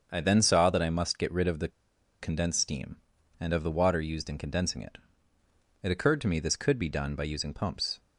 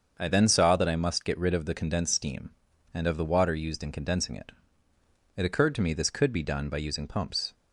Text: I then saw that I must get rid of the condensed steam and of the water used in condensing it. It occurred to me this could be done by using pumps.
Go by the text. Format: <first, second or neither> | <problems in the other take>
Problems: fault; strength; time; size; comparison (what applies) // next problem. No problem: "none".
second | starts louder than the rest; until 1.1 s; 7 dB; also in the second // pauses between "the" and "condensed"; noticeable; at 1.6 s; 0.52 s long